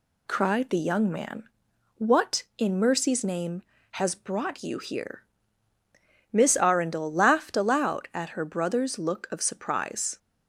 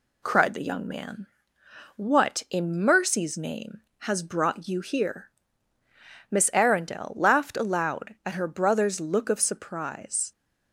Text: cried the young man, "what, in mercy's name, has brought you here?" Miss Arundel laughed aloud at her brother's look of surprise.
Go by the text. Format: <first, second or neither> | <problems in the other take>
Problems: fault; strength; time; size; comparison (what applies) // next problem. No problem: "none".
neither | none